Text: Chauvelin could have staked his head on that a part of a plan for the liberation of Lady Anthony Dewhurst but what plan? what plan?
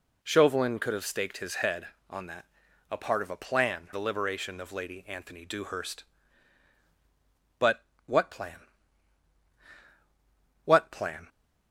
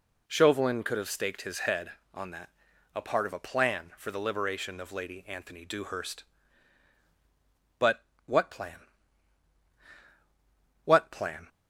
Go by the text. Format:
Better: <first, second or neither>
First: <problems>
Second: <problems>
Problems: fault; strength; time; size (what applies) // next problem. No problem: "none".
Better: second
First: pauses between "that" and "a"; at 2.4 s; 0.44 s long // skips "for"; at 3.9 s // pauses between "but" and "what"; slight; at 7.8 s; 0.24 s long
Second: pauses between "that" and "a"; at 2.4 s; 0.44 s long // pauses between "but" and "what"; slight; at 8.0 s; 0.24 s long